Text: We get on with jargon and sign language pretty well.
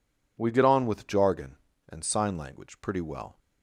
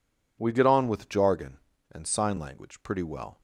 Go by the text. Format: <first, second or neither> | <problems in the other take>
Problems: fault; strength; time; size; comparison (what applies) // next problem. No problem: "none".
neither | none